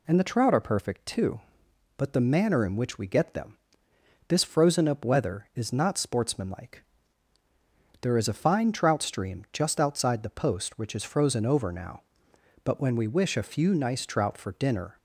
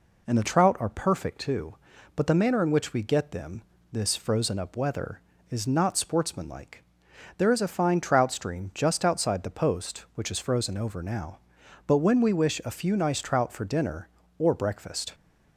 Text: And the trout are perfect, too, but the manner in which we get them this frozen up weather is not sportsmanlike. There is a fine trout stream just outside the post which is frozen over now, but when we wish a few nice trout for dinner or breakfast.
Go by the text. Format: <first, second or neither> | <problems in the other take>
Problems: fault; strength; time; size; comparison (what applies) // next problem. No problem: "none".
second | pauses between "them" and "this"; noticeable; at 3.5 s; 0.70 s long; slight in the second // stops before "or breakfast"; at 14.9 s